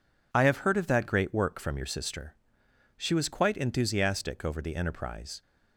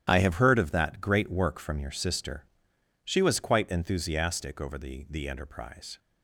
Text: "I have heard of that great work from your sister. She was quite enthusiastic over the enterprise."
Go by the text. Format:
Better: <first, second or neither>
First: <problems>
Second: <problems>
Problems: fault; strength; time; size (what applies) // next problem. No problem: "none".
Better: first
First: none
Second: starts louder than the rest; strong; until 1.1 s; 10.5 dB // says "the" twice; at 5.1 s